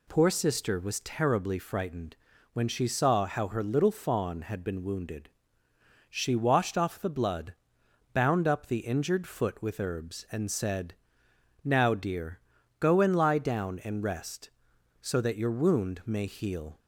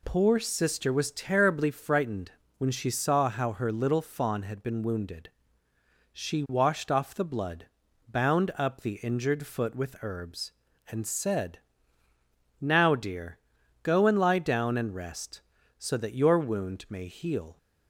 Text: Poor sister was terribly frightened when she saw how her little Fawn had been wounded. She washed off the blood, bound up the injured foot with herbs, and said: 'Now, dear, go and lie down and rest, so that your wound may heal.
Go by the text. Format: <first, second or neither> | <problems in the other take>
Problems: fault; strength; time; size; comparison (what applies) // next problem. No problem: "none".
neither | pauses between "frightened" and "when"; the same in both